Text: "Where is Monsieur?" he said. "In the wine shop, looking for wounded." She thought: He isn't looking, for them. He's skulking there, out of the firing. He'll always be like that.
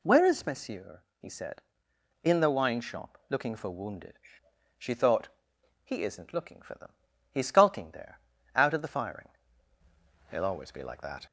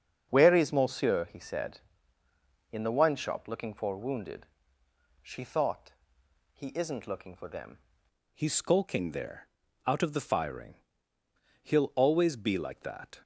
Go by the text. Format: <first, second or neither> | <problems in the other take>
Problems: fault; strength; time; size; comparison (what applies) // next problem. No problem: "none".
first | starts louder than the rest; until 1.3 s; 7 dB // changes voice at "He's"; from 8.3 s on; 4.9 s long